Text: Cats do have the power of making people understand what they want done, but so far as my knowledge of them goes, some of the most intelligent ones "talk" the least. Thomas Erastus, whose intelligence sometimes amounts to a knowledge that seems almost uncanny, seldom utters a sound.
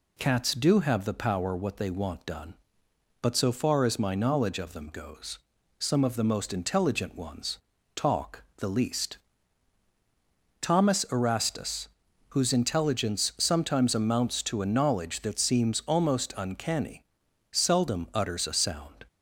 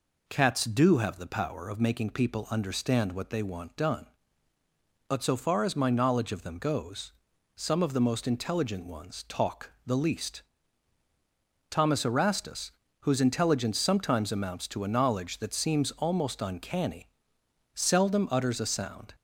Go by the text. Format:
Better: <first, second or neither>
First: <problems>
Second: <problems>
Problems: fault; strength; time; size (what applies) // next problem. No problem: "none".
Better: second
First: skips "of making people understand"; at 1.5 s // pauses between "ones" and "talk"; at 7.5 s; 0.38 s long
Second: none